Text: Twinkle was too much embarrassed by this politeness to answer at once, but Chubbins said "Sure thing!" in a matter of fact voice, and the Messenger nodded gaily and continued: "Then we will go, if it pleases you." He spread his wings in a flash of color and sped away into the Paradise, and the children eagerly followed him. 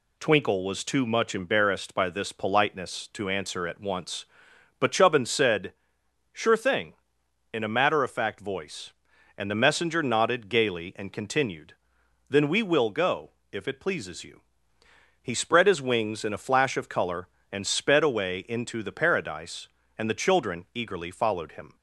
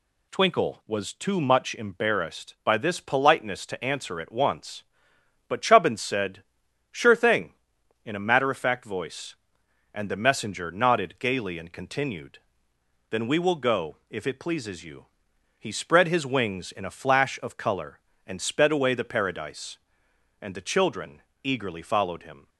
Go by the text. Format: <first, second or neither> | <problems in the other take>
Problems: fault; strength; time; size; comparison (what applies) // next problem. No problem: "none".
first | pauses between "said" and "Sure"; noticeable; at 6.4 s; 0.48 s long; noticeable in the first // skips "into"; at 18.9 s // pauses between "children" and "eagerly"; slight; at 21.2 s; 0.20 s long